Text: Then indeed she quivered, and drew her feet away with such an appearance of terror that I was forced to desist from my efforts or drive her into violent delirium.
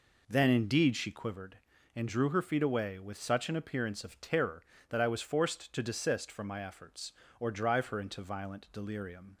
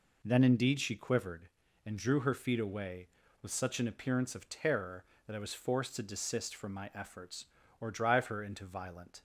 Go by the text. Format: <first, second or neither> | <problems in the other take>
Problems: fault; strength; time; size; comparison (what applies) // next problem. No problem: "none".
first | stops before "delirium"; at 9.1 s